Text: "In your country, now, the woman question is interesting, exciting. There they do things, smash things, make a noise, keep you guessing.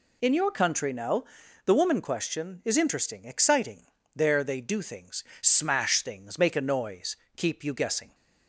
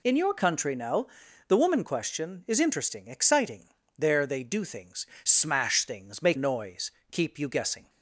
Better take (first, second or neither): first